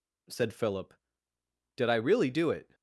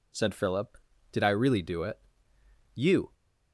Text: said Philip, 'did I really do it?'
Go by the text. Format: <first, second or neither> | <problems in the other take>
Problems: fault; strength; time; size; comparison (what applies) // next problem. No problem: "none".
first | goes on to say "You"; slight; from 2.7 s on; 0.34 s long